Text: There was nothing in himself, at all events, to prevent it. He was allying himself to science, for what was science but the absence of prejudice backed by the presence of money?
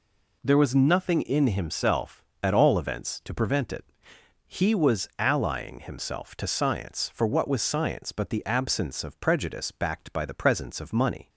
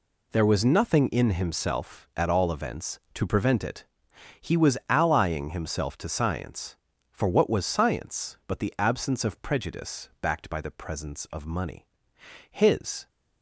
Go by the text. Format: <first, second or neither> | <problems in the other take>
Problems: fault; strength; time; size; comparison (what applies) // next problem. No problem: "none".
first | goes on to say "His"; from 12.5 s on; 0.58 s long